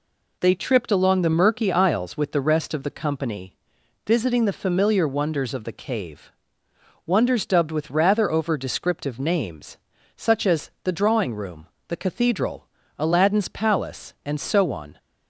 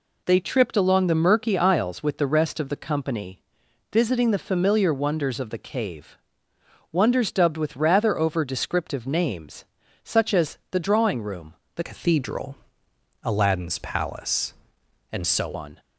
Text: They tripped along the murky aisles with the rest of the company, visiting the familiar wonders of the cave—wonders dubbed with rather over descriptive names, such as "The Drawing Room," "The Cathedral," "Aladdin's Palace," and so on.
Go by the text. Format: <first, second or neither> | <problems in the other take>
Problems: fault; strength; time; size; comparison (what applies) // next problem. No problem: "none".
first | changes voice from "Cathedral" to "so"; from 11.8 to 15.5 s; 3.7 s long